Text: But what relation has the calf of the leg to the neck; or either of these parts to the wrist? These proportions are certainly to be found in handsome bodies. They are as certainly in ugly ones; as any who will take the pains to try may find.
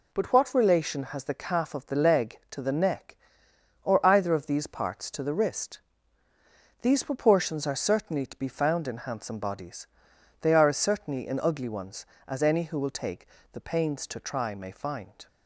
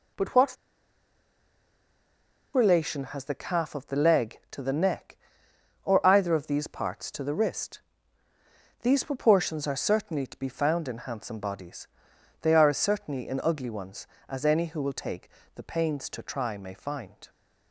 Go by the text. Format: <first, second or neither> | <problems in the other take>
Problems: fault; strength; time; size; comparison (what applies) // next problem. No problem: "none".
first | pauses between "what" and "relation"; strong; at 0.5 s; 1.9 s long // pauses between "take" and "the"; slight; at 15.2 s; 0.26 s long; slight in the first